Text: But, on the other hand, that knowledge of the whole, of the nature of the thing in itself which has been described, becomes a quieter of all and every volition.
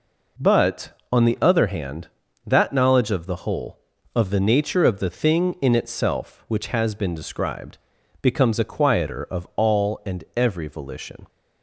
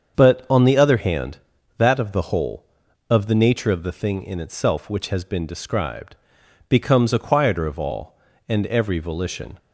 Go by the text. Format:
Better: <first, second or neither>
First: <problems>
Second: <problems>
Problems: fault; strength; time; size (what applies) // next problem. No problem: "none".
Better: first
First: none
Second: starts louder than the rest; strong; until 1.1 s; 7 dB // skips "knowledge"; at 1.9 s